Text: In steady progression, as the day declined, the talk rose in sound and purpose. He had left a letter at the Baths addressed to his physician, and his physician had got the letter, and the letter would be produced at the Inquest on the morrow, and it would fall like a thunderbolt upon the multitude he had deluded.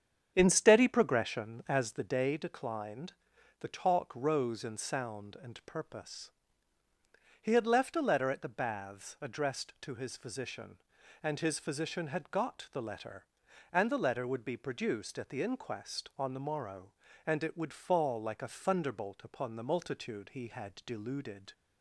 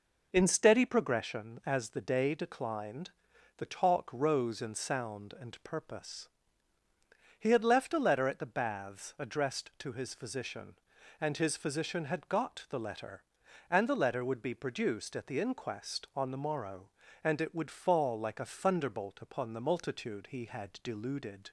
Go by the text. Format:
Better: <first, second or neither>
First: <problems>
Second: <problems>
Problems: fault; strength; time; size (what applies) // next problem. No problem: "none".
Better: second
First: starts louder than the rest; strong; until 2.2 s; 8 dB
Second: none